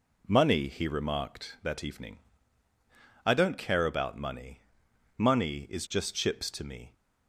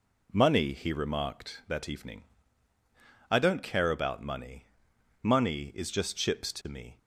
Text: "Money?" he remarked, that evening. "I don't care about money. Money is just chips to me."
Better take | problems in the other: neither | none

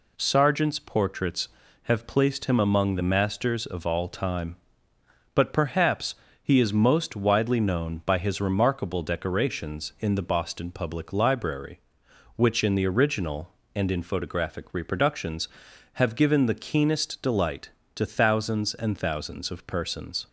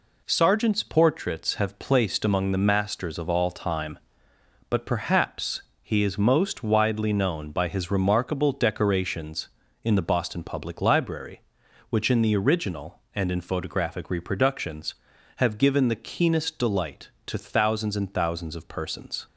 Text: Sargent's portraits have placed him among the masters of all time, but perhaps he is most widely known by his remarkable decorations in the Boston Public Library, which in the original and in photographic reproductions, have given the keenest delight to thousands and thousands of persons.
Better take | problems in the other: first | skips "him"; at 2.2 s // pauses between "perhaps" and "he"; slight; at 5.6 s; 0.18 s long; slight in the first

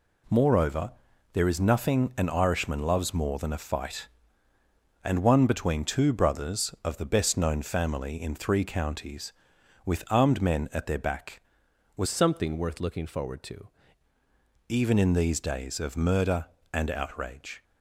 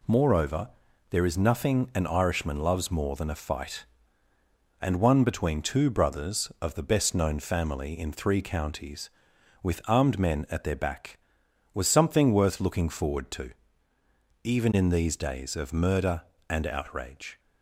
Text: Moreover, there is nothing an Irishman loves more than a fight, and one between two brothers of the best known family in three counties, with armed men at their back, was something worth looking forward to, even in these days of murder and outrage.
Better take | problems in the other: second | changes voice from "something" to "to"; from 12.0 to 13.6 s; 1.6 s long

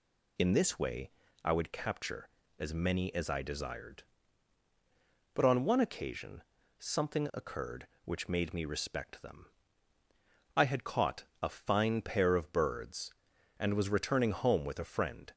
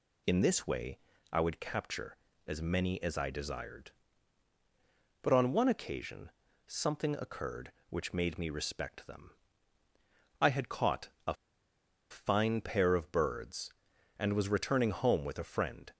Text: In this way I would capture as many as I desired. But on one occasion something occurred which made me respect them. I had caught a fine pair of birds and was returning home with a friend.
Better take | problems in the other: first | pauses between "way" and "I"; slight; at 0.9 s; 0.32 s long; slight in the first // pauses between "occasion" and "something"; slight; at 6.3 s; 0.36 s long; slight in the first // pauses between "caught" and "a"; slight; at 11.0 s; 0.18 s long; slight in the first // pauses between "a" and "fine"; noticeable; at 11.3 s; 0.76 s long

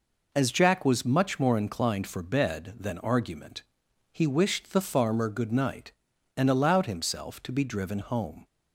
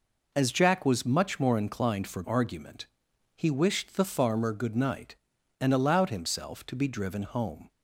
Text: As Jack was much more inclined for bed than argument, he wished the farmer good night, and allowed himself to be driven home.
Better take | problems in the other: first | skips "bed than"; at 2.2 s

